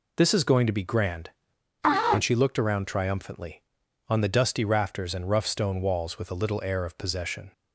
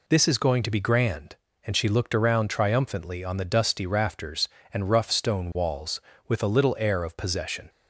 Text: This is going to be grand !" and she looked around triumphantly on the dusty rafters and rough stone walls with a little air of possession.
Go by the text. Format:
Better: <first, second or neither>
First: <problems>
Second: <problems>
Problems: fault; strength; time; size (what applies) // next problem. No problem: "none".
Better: neither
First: none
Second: none